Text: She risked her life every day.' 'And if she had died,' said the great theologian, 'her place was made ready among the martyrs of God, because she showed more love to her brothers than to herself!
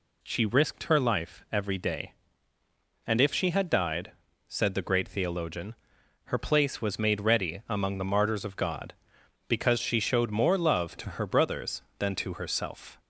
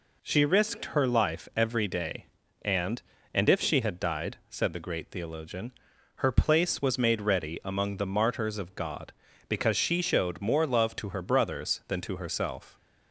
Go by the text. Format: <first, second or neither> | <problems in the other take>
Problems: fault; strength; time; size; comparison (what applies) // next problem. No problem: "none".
first | says "And" twice; at 3.3 s